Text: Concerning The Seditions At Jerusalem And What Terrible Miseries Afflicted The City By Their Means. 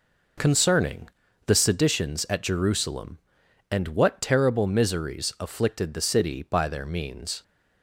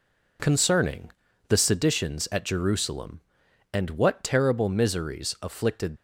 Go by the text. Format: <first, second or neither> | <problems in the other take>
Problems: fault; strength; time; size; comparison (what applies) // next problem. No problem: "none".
first | pauses between "Concerning" and "The"; at 1.1 s; 0.38 s long; also in the first // stops before "The City By Their Means"; at 5.9 s